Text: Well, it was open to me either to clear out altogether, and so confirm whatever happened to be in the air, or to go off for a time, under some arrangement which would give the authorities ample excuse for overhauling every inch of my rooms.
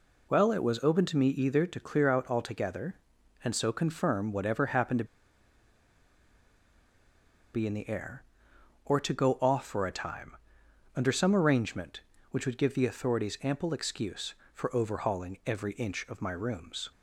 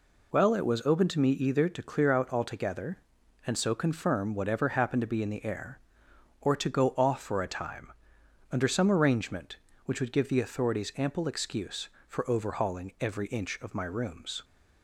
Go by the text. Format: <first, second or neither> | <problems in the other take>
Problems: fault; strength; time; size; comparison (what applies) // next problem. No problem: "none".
second | pauses between "to" and "be"; strong; at 5.0 s; 2.4 s long